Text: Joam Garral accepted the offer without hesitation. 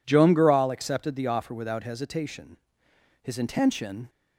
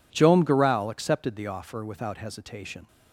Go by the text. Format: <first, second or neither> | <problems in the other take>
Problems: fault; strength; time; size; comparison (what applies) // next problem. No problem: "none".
second | goes on to say "His intention"; noticeable; from 3.2 s on; 0.88 s long